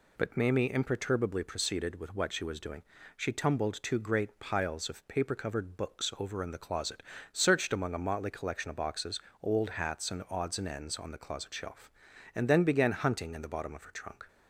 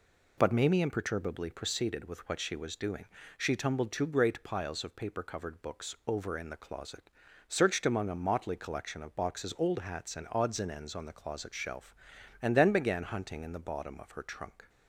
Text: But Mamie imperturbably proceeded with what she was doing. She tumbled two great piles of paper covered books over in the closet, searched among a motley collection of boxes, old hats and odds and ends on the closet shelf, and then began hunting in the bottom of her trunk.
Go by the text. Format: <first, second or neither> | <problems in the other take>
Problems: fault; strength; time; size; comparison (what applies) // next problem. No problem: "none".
neither | none